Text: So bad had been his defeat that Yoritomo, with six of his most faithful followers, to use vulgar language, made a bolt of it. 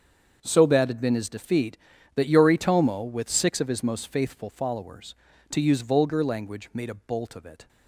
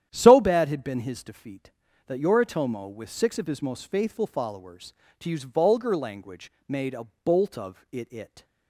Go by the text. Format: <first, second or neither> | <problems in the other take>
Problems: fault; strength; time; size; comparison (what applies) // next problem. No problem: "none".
first | starts louder than the rest; strong; until 1.1 s; 10.5 dB; also in the first // pauses between "a" and "bolt"; slight; at 7.0 s; 0.16 s long // says "it" twice; at 8.1 s